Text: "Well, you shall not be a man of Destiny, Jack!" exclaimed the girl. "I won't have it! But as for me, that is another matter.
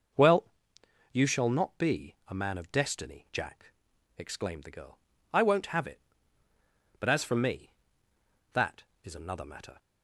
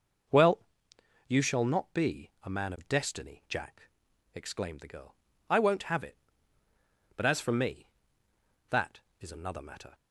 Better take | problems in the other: neither | none

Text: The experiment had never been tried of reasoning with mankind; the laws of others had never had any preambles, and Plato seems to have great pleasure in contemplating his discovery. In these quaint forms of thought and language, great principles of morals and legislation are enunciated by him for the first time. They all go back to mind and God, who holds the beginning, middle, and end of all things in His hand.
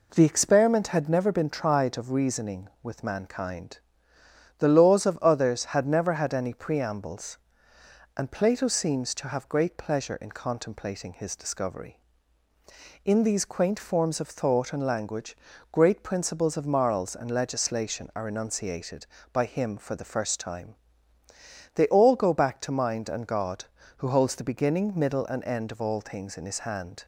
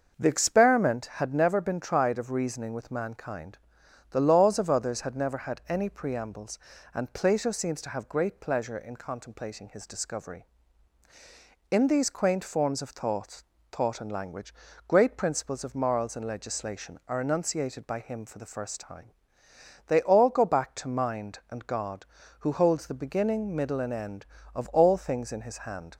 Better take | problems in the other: first | starts louder than the rest; until 1.2 s; 6.5 dB // says "thought" twice; at 13.7 s

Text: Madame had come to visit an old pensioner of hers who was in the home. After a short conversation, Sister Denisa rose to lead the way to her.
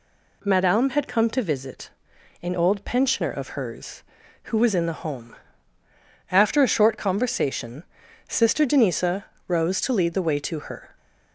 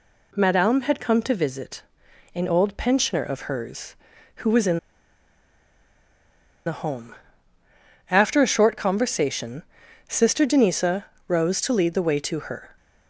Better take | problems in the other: first | pauses between "visit" and "an"; noticeable; at 1.8 s; 0.50 s long; noticeable in the first // pauses between "in" and "the"; strong; at 4.7 s; 1.8 s long // pauses between "Denisa" and "rose"; slight; at 11.0 s; 0.24 s long; slight in the first

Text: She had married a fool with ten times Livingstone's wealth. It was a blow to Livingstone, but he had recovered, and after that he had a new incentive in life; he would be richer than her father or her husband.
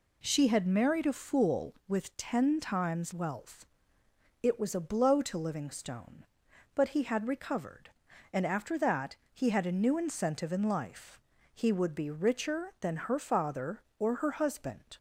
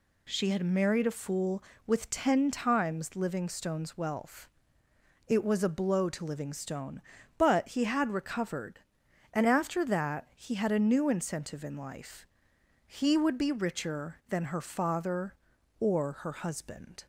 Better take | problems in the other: second | skips "Livingstone's"; at 3.1 s // pauses between "that" and "he"; slight; at 9.1 s; 0.20 s long

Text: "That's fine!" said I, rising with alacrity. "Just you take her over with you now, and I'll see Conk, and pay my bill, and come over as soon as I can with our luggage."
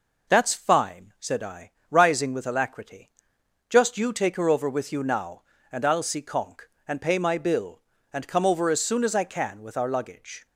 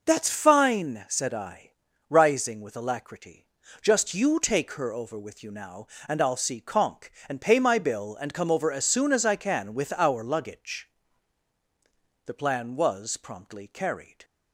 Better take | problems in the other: first | goes on to say "The plan was promptly carried"; strong; from 12.2 s on; 1.9 s long

